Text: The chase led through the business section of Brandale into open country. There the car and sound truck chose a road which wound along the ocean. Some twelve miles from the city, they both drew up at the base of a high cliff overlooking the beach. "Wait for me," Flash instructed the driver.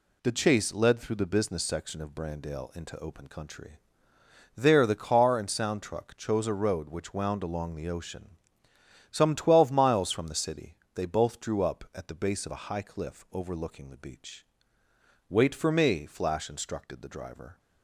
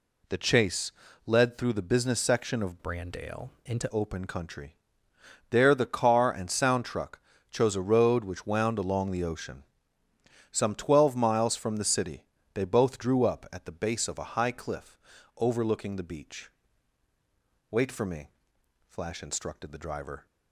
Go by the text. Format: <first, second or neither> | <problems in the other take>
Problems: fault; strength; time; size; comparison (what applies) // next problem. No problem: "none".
first | pauses between "chase" and "led"; slight; at 0.9 s; 0.34 s long // changes voice from "Brandale" to "into"; from 2.8 to 3.8 s; 1.0 s long // pauses between "Brandale" and "into"; slight; at 3.4 s; 0.16 s long // pauses between "truck" and "chose"; slight; at 7.1 s; 0.30 s long // pauses between "cliff" and "overlooking"; at 14.9 s; 0.40 s long